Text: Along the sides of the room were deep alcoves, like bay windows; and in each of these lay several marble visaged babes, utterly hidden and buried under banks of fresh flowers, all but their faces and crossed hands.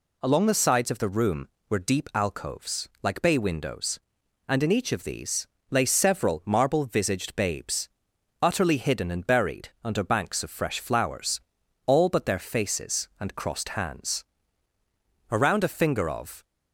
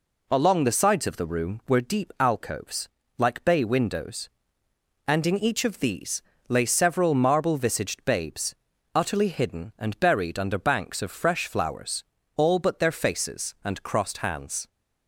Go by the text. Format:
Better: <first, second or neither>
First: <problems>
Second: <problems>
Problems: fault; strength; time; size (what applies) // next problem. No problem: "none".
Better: second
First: pauses between "these" and "lay"; slight; at 5.4 s; 0.24 s long // pauses between "buried" and "under"; slight; at 9.6 s; 0.16 s long // goes on to say "Around a finger of"; noticeable; from 15.2 s on; 1.1 s long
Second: pauses between "these" and "lay"; slight; at 6.1 s; 0.28 s long